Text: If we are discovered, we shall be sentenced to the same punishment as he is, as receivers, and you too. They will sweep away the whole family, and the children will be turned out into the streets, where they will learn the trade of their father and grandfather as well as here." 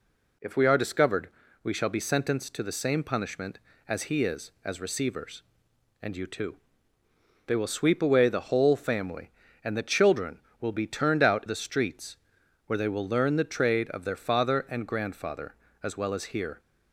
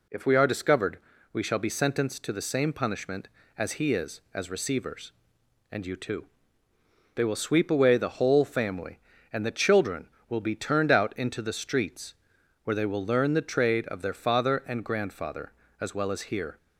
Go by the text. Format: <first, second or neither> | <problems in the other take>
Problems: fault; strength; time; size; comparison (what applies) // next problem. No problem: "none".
second | skips "into"; at 11.4 s